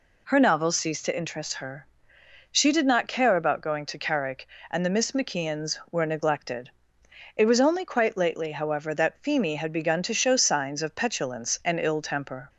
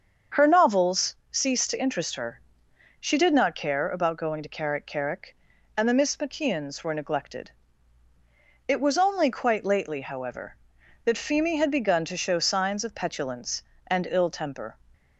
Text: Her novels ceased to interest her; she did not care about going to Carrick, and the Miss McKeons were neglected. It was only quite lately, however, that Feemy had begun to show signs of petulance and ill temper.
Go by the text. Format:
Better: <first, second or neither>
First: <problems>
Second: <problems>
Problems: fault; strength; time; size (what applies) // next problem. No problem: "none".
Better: first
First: none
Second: starts louder than the rest; until 1.5 s; 7 dB // pauses between "novels" and "ceased"; slight; at 1.1 s; 0.16 s long // says "Carrick" twice; at 4.8 s